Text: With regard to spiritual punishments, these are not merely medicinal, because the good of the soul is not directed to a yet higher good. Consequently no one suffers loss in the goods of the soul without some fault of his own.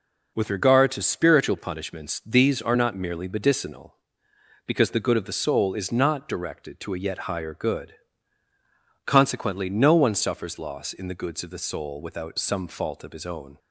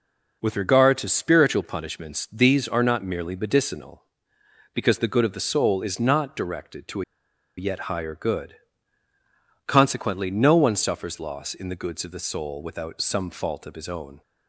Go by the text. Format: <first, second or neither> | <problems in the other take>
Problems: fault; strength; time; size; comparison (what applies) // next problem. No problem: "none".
first | pauses between "a" and "yet"; noticeable; at 7.0 s; 0.54 s long